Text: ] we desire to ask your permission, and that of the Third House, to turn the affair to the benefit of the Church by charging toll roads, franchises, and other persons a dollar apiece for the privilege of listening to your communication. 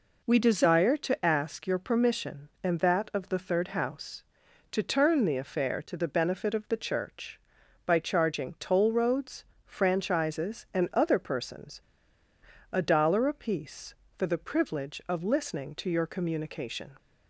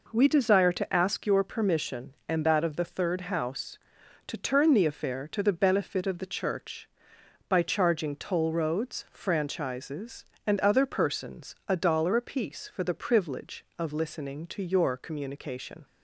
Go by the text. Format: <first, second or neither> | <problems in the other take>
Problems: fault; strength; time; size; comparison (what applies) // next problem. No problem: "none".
second | pauses between "persons" and "a"; noticeable; at 11.8 s; 0.90 s long